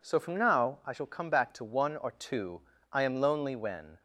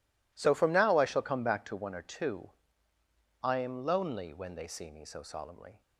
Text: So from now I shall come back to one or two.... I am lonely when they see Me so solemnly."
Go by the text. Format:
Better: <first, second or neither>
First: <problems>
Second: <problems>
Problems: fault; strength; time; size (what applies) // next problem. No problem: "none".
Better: second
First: stops before "they see Me so solemnly"; at 3.9 s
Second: none